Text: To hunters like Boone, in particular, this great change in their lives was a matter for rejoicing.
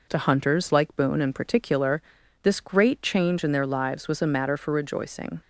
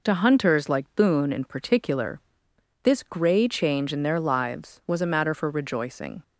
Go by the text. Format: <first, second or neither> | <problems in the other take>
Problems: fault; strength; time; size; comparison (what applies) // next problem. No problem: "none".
first | says "grey" for "great"; at 3.0 s